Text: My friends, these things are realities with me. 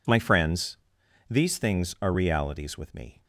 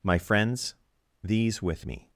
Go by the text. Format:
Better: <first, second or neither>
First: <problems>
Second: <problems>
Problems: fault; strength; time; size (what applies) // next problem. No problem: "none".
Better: first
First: none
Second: skips "things are realities"; at 1.6 s